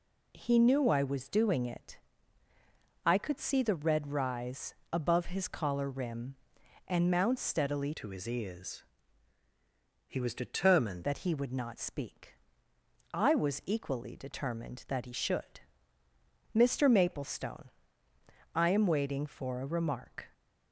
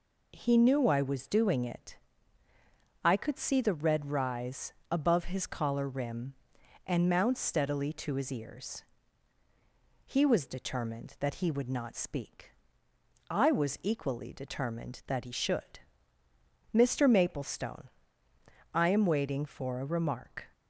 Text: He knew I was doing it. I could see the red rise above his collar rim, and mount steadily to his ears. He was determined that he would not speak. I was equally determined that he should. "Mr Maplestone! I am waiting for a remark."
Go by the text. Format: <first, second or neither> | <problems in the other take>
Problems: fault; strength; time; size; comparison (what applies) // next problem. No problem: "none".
second | pauses between "rise" and "above"; slight; at 4.7 s; 0.18 s long; slight in the second // changes voice from "to" to "determined"; from 7.9 to 11.0 s; 3.1 s long